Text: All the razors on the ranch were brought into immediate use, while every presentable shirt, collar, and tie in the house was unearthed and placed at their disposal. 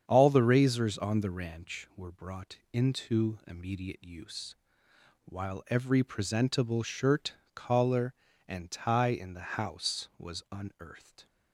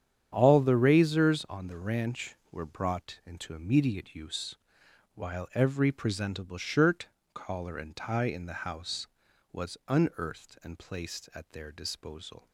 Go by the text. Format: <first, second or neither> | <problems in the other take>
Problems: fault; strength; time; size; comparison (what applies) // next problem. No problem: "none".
second | starts louder than the rest; strong; until 1.0 s; 8 dB; strong in the second // stops before "and placed at their disposal"; at 11.2 s